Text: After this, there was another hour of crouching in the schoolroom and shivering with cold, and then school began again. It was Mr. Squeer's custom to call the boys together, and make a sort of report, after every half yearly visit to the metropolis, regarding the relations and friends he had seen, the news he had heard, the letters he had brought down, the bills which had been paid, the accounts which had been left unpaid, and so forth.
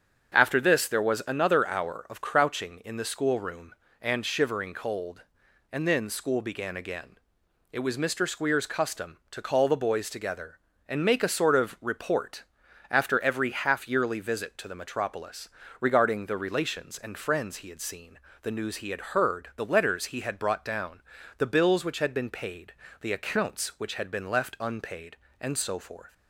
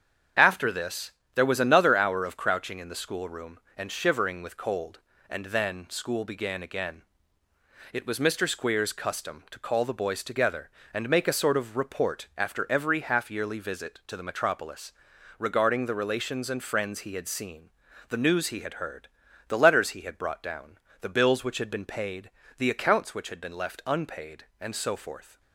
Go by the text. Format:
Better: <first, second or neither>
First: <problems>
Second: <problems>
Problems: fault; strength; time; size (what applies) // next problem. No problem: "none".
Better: second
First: starts louder than the rest; strong; until 1.3 s; 7 dB // skips "with"; at 4.7 s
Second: starts louder than the rest; strong; until 1.6 s; 7.5 dB